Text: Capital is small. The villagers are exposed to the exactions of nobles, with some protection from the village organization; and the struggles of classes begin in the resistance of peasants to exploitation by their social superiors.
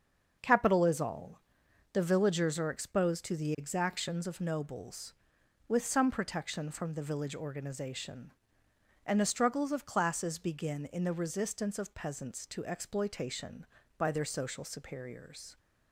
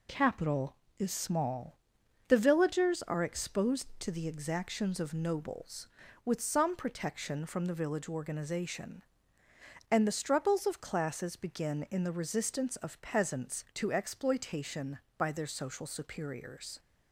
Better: second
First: starts louder than the rest; until 1.4 s; 6.5 dB // says "all" for "small"; at 1.0 s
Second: none

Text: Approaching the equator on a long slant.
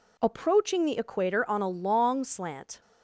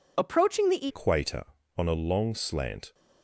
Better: first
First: none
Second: changes voice at "equator"; from 0.8 s on; 2.1 s long

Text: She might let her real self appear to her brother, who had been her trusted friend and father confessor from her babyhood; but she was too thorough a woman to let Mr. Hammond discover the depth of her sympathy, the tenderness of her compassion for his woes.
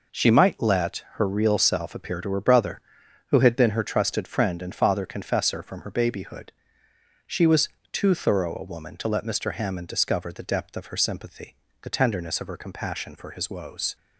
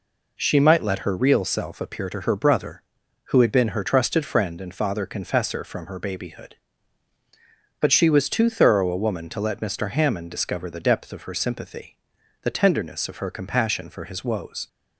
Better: second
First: skips "but"; at 6.8 s // pauses between "was" and "too"; slight; at 7.6 s; 0.22 s long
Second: none

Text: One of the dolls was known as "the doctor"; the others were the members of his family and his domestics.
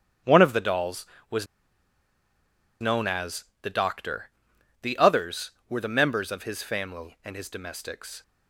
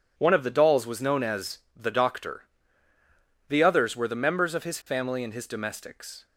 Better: second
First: starts louder than the rest; strong; until 2.8 s; 8 dB // pauses between "was" and "known"; strong; at 1.4 s; 1.3 s long // pauses between "as" and "the"; slight; at 3.4 s; 0.20 s long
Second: pauses between "as" and "the"; slight; at 1.5 s; 0.16 s long

